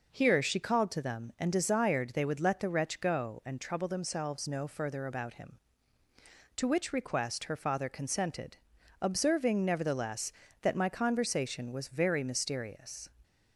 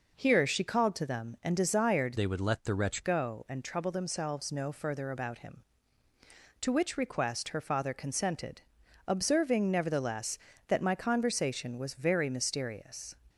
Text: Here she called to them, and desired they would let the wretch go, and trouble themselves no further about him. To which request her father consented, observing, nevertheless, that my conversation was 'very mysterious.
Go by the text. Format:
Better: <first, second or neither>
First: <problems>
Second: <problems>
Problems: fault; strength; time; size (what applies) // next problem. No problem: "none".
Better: first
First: none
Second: changes voice from "they" to "wretch"; from 2.1 to 3.0 s; 0.9 s long